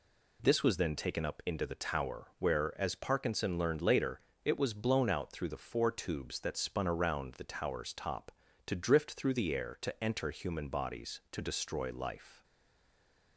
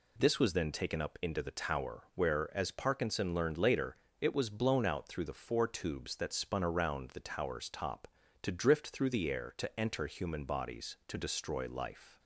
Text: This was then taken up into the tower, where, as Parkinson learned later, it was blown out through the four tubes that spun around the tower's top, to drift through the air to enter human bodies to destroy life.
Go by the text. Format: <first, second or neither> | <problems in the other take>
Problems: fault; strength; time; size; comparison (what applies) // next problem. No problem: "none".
second | stays silent after the last word; from 12.4 s on; 0.9 s long